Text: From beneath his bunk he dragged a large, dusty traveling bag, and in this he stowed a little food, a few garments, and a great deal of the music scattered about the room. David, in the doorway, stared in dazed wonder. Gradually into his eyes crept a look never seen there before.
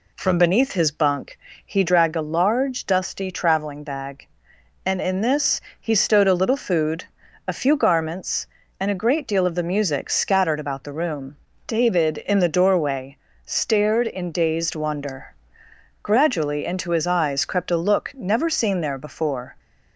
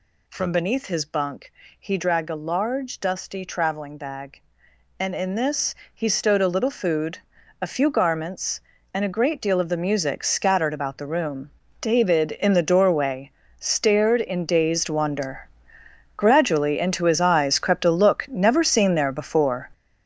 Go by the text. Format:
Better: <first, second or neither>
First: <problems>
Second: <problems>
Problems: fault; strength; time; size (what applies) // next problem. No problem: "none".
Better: first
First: pauses between "bunk" and "he"; slight; at 1.3 s; 0.26 s long // pauses between "this" and "he"; slight; at 5.5 s; 0.22 s long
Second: gets louder; strong; throughout; 9 dB // pauses between "bunk" and "he"; slight; at 1.5 s; 0.26 s long // pauses between "this" and "he"; slight; at 5.7 s; 0.22 s long